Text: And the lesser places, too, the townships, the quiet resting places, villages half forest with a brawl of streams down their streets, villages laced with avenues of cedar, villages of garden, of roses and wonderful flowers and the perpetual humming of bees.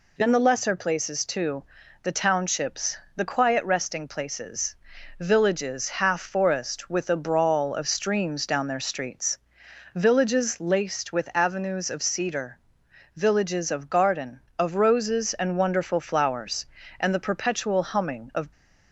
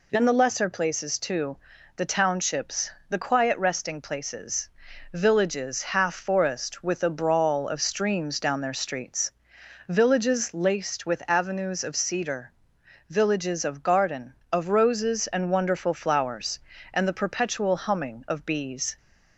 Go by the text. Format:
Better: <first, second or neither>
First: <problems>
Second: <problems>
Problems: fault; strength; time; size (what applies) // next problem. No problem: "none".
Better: second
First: stops before "bees"; at 18.5 s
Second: none